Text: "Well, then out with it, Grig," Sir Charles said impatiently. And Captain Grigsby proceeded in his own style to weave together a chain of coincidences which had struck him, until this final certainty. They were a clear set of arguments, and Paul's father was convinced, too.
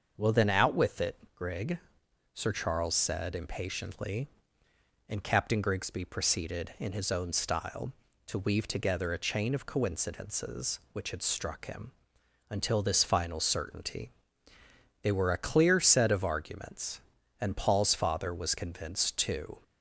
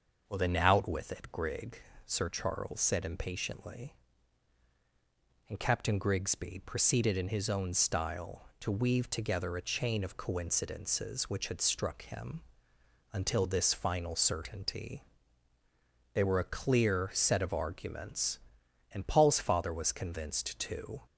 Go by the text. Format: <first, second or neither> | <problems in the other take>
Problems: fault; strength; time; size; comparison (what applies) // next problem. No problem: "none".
neither | starts louder than the rest; the same in both